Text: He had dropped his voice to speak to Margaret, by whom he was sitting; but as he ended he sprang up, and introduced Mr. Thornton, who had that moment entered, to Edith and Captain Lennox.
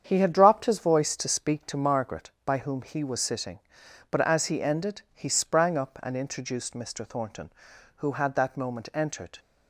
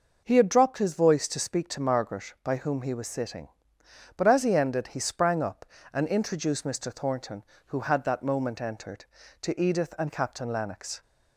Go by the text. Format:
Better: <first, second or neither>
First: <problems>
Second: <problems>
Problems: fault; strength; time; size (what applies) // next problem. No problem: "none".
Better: second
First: starts louder than the rest; strong; until 1.0 s; 8 dB // stops before "to Edith and Captain Lennox"; at 9.3 s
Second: none